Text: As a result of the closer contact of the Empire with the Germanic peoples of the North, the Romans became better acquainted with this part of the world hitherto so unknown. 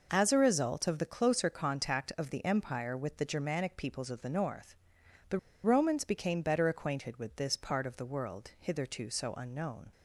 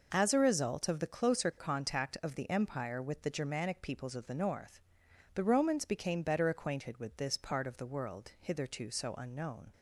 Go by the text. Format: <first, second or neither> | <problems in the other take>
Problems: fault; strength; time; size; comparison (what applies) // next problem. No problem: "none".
second | pauses between "the" and "Romans"; slight; at 5.3 s; 0.24 s long